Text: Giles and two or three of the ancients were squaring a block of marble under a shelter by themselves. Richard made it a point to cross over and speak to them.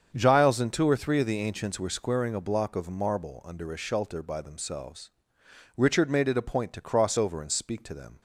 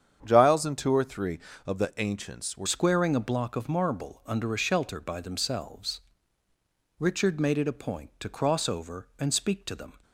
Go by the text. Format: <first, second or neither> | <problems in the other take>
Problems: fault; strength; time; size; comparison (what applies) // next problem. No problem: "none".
first | starts louder than the rest; strong; until 1.2 s; 8 dB; strong in the first // changes voice at "squaring"; from 2.6 s on; 7.3 s long